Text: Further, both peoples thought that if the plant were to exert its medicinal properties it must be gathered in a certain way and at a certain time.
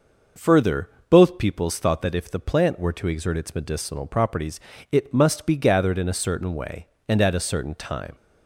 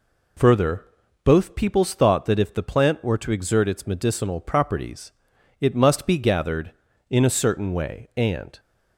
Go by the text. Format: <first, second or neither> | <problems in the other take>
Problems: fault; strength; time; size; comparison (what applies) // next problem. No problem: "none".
first | pauses between "properties" and "it"; noticeable; at 5.0 s; 0.50 s long; slight in the first // stops before "at a certain time"; at 8.5 s